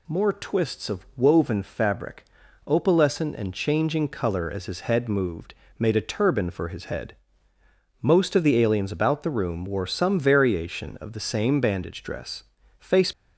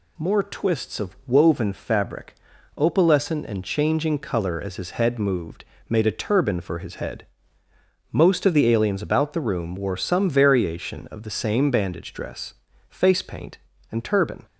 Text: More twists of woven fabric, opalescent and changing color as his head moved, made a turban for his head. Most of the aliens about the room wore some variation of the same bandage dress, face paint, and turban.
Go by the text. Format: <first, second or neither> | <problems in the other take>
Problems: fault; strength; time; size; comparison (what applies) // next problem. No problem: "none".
second | stops before "paint and turban"; at 13.1 s